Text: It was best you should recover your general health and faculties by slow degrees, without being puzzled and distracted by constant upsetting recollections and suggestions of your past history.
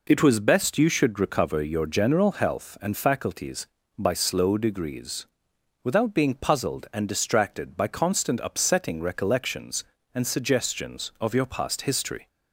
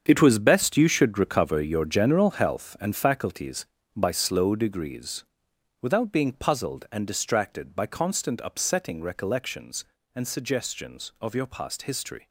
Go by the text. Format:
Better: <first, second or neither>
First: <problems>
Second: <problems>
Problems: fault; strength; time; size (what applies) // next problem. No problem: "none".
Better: first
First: none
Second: gets quieter; strong; throughout; 11.5 dB